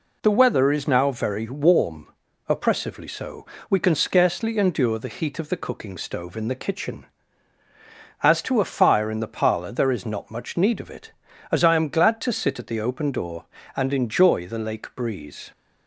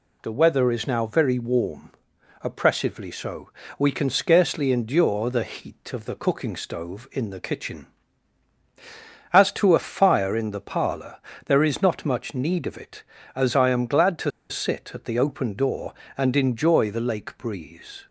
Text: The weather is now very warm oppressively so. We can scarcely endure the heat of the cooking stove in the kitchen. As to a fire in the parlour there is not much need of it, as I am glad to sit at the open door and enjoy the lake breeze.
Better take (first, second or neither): first